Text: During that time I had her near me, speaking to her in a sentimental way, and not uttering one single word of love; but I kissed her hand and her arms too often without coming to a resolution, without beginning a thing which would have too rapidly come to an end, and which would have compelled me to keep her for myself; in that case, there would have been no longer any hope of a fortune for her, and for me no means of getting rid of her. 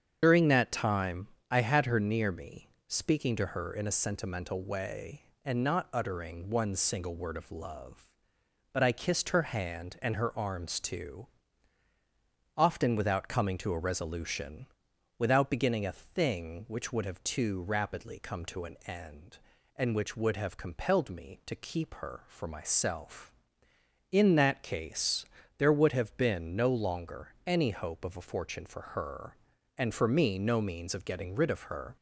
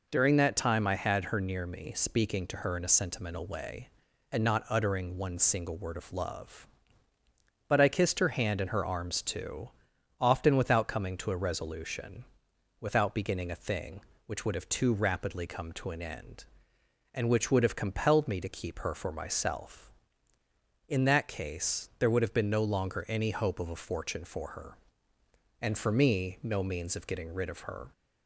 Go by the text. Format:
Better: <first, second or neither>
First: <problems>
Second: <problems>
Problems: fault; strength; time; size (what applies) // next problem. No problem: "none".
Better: second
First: loses the start of "During"; at 0.2 s; 50 ms // starts louder than the rest; strong; until 1.2 s; 7.5 dB // pauses between "time" and "I"; slight; at 1.2 s; 0.22 s long // pauses between "too" and "often"; strong; at 11.2 s; 1.2 s long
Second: pauses between "too" and "often"; noticeable; at 9.6 s; 0.50 s long